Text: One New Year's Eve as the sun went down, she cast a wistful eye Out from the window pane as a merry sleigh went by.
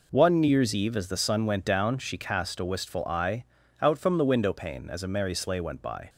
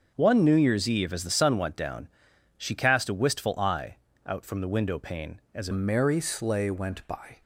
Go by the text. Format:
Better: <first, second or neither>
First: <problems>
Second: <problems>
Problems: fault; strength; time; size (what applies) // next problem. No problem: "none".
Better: first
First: pauses between "eye" and "Out"; slight; at 3.4 s; 0.36 s long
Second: starts louder than the rest; until 1.1 s; 6.5 dB // pauses between "eye" and "Out"; slight; at 3.9 s; 0.30 s long // changes voice at "merry"; from 5.7 s on; 1.7 s long